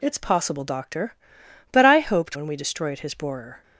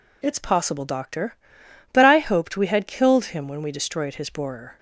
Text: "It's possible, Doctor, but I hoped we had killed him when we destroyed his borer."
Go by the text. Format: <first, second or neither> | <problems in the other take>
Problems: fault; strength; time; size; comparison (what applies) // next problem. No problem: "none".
second | skips "we had killed him"; at 2.3 s